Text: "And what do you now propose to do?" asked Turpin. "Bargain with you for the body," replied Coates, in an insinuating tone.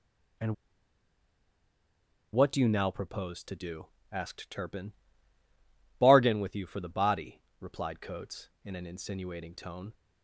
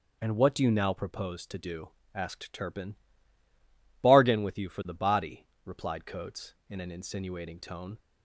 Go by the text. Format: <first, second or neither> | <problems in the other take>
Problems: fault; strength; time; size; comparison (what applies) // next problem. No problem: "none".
second | pauses between "And" and "what"; strong; at 0.5 s; 1.7 s long